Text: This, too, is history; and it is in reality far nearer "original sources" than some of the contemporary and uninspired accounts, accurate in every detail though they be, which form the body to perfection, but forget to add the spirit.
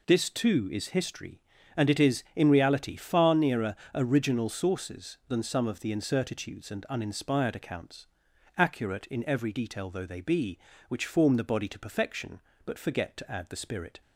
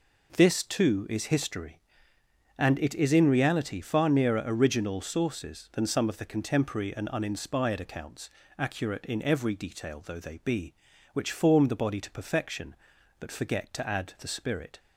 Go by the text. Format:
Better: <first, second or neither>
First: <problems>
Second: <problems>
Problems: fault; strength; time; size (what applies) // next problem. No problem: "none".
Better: second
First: pauses between "nearer" and "original"; slight; at 3.7 s; 0.20 s long // says "incertitudes" for "contemporary"; at 5.9 s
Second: none